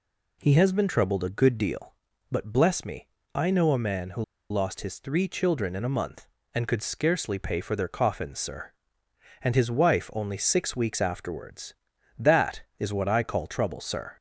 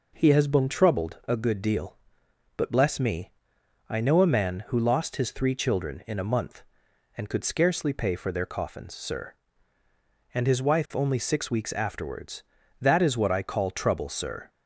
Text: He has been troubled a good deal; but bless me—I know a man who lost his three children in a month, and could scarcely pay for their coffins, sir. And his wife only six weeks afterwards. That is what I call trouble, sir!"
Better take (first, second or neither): second